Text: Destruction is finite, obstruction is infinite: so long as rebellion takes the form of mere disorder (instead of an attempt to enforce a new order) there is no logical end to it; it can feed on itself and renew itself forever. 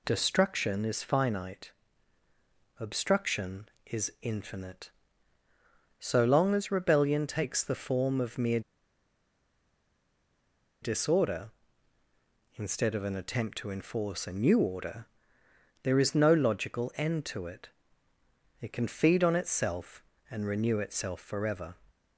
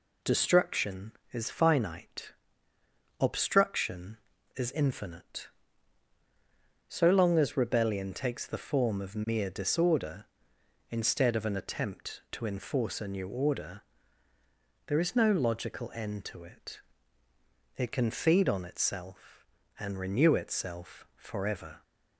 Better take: second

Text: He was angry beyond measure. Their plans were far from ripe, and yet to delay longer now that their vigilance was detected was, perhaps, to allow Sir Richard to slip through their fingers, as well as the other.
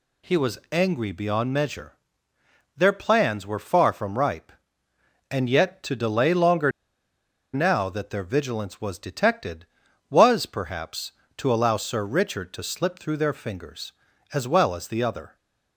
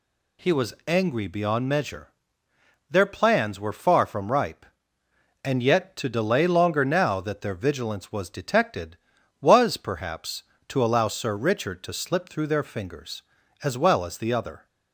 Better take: second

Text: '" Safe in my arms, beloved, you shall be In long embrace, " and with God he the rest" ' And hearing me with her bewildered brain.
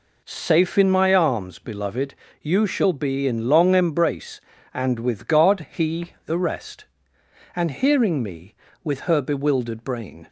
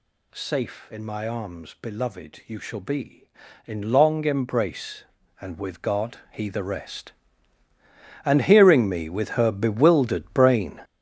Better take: first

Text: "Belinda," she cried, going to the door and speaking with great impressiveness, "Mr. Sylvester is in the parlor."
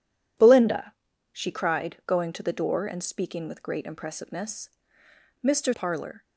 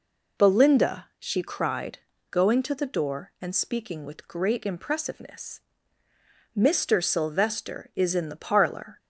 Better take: second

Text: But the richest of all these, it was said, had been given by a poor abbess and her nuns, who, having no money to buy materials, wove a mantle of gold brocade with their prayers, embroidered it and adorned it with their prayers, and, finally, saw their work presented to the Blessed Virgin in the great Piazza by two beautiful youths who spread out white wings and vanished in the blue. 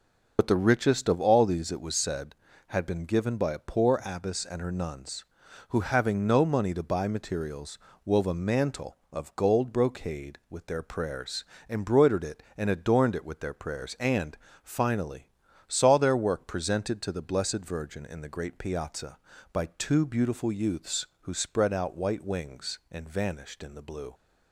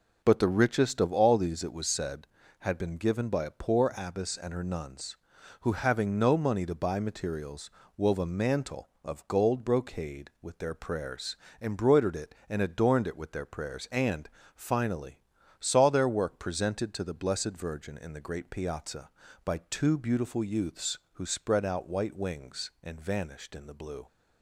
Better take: second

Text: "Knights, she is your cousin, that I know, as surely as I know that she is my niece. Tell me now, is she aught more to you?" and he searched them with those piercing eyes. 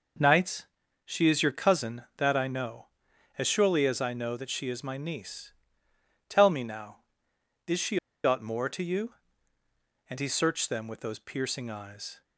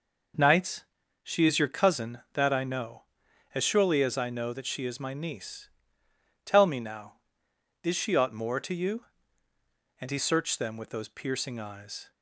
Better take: second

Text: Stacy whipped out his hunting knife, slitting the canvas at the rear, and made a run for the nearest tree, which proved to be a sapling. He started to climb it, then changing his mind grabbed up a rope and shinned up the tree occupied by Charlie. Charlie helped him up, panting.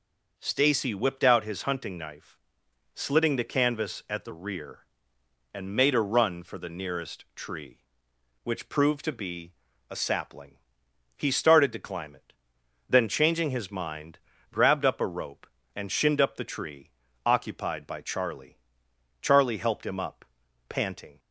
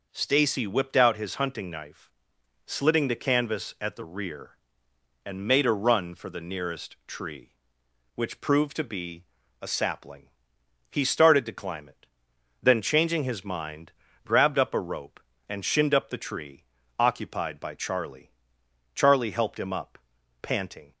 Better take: neither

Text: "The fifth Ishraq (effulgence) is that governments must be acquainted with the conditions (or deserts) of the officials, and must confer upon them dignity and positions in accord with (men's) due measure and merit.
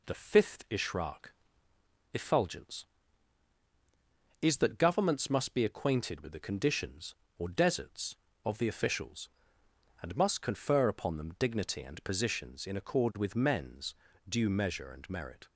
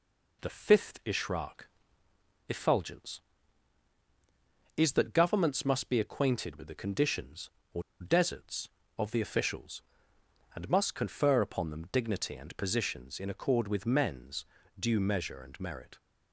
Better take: first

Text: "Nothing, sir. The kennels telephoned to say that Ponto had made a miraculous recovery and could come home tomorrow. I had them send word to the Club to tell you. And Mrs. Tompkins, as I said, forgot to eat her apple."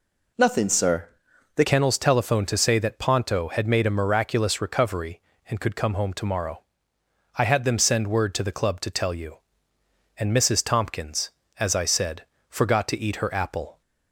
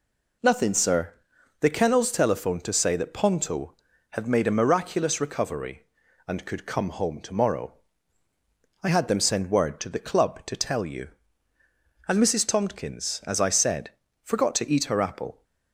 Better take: second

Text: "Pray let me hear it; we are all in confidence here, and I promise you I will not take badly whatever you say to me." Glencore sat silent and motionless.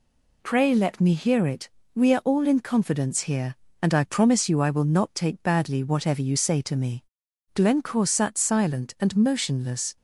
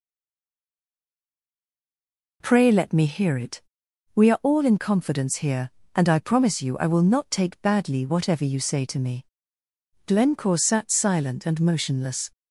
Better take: first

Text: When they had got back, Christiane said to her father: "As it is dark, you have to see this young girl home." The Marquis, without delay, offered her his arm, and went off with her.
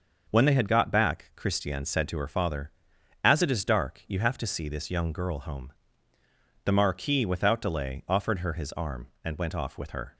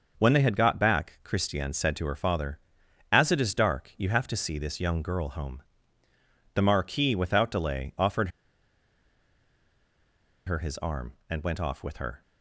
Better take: first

